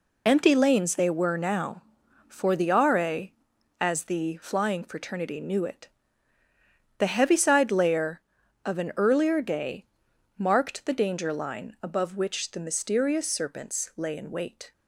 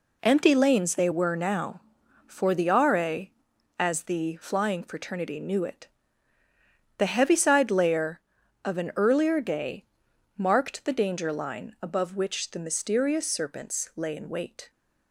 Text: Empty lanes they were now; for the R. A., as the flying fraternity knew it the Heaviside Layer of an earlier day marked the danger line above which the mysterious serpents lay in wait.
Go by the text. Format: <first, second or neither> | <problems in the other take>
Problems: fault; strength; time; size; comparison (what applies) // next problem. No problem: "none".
second | loses the start of "Empty"; at 0.2 s; 45 ms // pauses between "it" and "the"; at 5.8 s; 1.1 s long; also in the second // pauses between "day" and "marked"; noticeable; at 9.8 s; 0.52 s long; noticeable in the second